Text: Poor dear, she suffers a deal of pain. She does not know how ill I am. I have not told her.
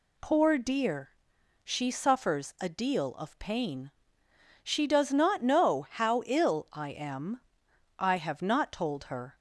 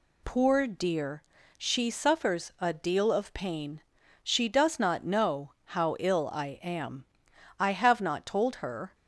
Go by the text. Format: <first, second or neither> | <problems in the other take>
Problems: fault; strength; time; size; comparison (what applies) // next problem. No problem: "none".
neither | none